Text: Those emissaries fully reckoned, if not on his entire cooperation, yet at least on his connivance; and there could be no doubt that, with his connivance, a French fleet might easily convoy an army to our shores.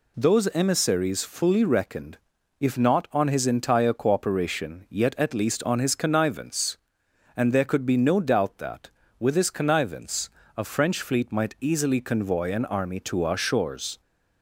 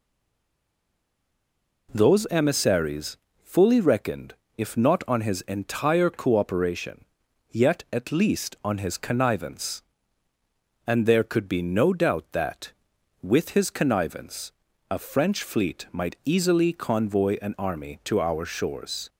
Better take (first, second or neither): first